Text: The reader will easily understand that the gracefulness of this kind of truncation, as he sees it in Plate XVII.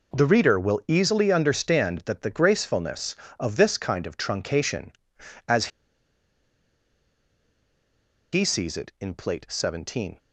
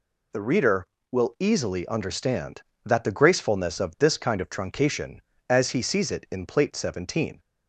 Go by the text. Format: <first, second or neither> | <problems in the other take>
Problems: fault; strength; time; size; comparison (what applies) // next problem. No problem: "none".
second | pauses between "as" and "he"; strong; at 5.6 s; 2.6 s long